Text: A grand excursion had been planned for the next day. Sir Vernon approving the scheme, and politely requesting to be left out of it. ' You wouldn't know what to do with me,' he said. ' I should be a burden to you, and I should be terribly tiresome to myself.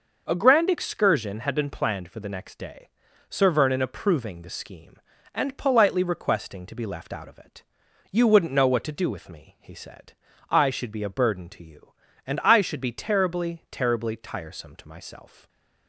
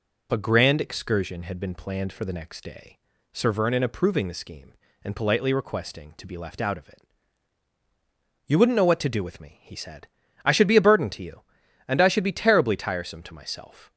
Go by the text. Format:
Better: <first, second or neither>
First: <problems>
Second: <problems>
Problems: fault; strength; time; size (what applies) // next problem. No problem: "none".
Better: second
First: says "terribly" twice; at 13.7 s // stays silent after the last word; slight; from 15.2 s on; 0.6 s long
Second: none